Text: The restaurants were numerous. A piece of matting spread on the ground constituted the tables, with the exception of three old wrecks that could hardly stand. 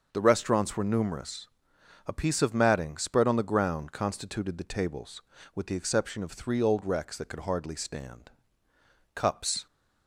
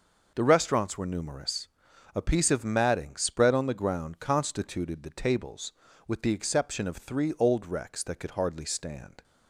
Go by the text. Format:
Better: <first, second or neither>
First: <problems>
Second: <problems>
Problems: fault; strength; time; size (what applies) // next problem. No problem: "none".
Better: second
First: starts louder than the rest; until 1.1 s; 6.5 dB // goes on to say "Cups"; from 9.1 s on; 0.52 s long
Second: none